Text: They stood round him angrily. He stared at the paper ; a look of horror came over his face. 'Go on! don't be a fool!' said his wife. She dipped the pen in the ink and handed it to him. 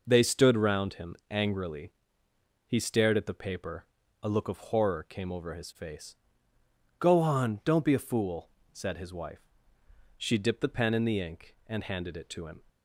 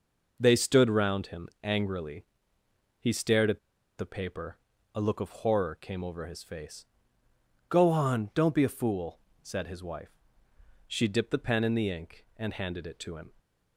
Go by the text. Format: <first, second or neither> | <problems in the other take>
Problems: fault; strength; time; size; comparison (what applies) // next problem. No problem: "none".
first | pauses between "at" and "the"; at 3.5 s; 0.39 s long